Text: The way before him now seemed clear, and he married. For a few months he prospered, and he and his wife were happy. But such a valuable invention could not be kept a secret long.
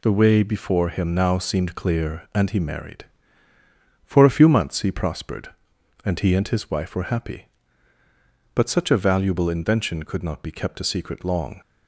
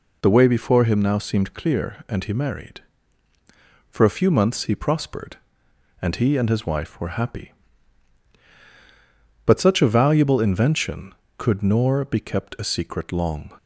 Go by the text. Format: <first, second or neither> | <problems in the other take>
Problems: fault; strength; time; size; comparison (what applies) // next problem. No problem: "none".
first | says "nor" for "not"; at 11.6 s